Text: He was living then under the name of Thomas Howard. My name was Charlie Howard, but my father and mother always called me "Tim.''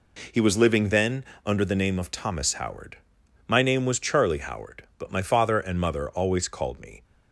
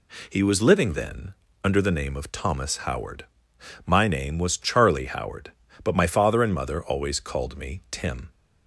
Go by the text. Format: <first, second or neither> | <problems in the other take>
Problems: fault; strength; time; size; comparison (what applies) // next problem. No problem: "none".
second | pauses between "then" and "under"; slight; at 1.2 s; 0.22 s long; slight in the second // stops before "Tim"; at 7.0 s